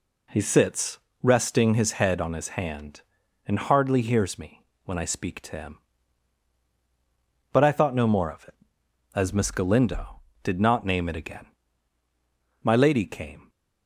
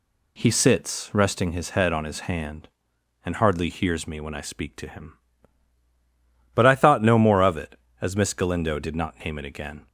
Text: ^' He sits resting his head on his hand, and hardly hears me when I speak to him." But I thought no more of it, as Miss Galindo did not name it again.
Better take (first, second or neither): second